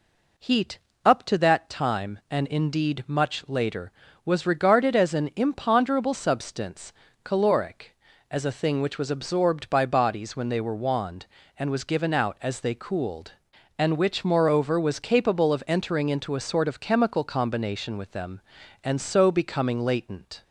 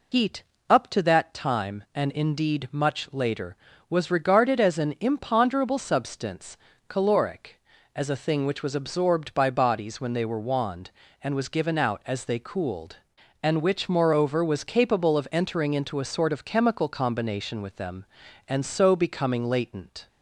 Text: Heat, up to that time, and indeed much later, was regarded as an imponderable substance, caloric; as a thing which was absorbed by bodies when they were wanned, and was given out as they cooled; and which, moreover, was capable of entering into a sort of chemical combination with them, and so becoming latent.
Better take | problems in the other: first | loses the start of "Heat"; at 0.1 s; 85 ms

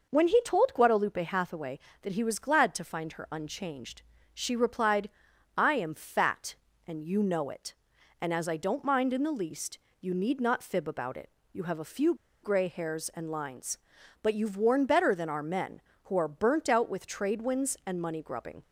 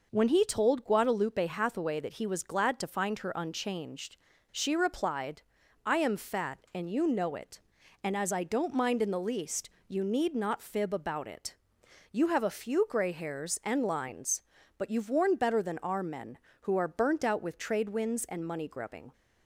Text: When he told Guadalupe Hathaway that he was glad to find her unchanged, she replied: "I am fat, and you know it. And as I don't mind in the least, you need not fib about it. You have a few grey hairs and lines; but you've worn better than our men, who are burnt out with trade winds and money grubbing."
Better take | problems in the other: second | pauses between "few" and "grey"; slight; at 12.1 s; 0.28 s long

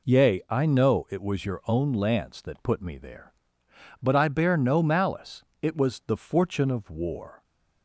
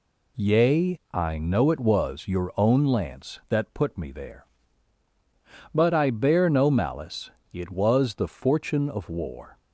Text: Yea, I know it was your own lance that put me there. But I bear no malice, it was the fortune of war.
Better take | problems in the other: neither | none

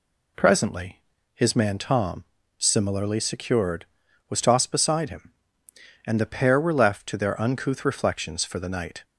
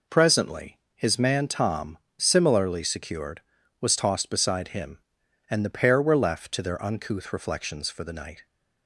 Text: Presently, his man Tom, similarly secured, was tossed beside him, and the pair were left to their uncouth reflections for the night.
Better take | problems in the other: neither | none

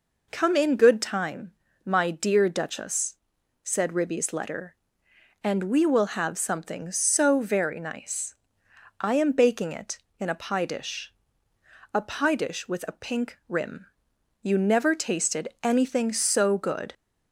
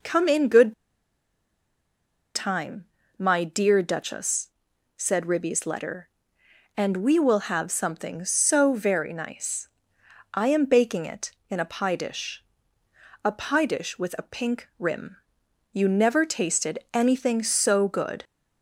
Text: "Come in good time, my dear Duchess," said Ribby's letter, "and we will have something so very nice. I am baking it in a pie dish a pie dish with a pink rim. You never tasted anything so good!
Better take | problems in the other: first | pauses between "good" and "time"; strong; at 0.7 s; 1.6 s long // pauses between "dish" and "a"; noticeable; at 12.4 s; 0.80 s long; noticeable in the first

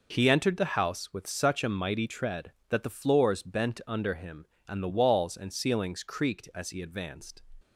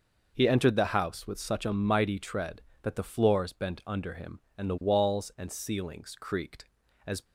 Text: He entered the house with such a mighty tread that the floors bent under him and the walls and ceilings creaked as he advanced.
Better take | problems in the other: first | stops before "he advanced"; at 7.2 s

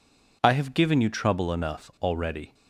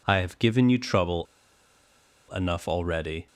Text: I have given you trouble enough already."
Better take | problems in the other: first | pauses between "trouble" and "enough"; at 1.2 s; 1.0 s long

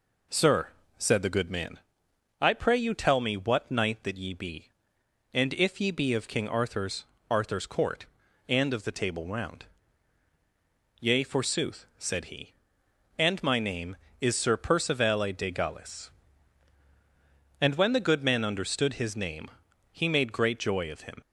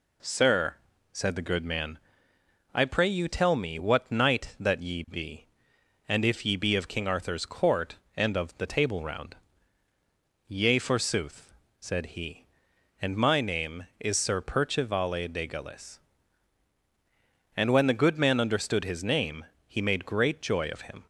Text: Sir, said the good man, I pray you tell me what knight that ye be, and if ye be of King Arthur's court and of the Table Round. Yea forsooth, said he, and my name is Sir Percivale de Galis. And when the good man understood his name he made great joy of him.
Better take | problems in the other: second | says "Arthur's" twice; at 7.2 s // pauses between "name" and "he"; at 19.4 s; 0.42 s long; slight in the second

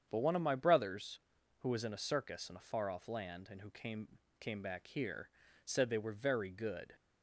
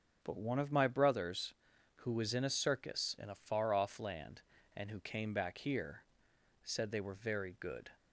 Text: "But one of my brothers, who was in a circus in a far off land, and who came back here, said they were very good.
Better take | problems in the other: second | starts louder than the rest; strong; until 1.1 s; 8 dB; also in the second // says "came" twice; at 4.3 s

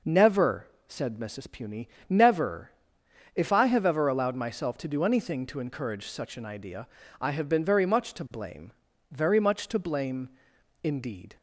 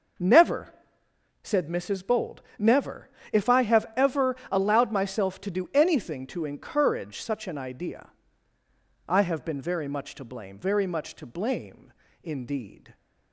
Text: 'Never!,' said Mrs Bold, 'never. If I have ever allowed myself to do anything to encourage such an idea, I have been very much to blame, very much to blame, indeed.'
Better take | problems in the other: second | says "Puny" for "Bold"; at 1.4 s

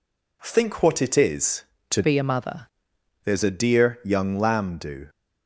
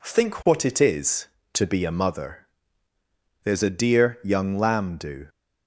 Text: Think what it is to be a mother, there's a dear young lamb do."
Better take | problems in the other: second | changes voice from "be" to "mother"; from 2.0 to 2.6 s; 0.6 s long

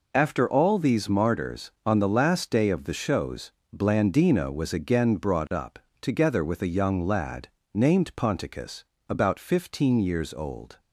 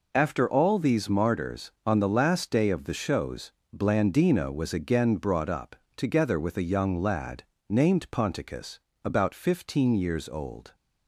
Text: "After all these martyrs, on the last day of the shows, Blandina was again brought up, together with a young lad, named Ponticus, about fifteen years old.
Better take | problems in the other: neither | none

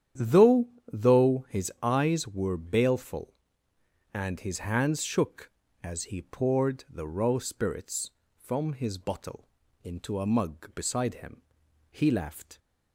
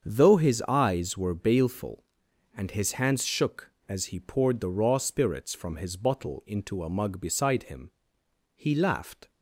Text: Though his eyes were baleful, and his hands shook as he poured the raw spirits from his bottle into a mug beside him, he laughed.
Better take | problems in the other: second | starts louder than the rest; strong; until 1.4 s; 9.5 dB; strong in the second // says "Though" twice; at 0.9 s // pauses between "bottle" and "into"; at 9.4 s; 0.38 s long

